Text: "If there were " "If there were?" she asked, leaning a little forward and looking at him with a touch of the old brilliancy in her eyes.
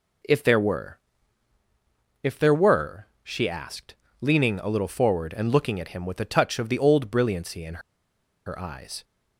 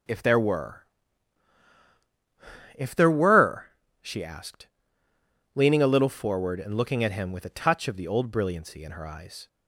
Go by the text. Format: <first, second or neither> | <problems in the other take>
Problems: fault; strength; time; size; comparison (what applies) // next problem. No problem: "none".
second | pauses between "in" and "her"; noticeable; at 7.8 s; 0.65 s long